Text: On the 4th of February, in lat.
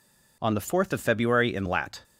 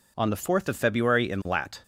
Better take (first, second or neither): neither